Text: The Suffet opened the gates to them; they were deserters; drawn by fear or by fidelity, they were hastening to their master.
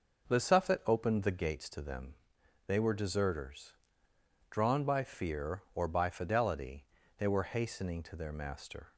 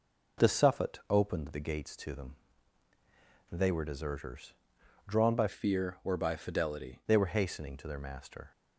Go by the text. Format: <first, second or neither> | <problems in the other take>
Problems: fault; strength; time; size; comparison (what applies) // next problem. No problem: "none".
first | changes voice from "fear" to "fidelity"; from 5.4 to 7.0 s; 1.6 s long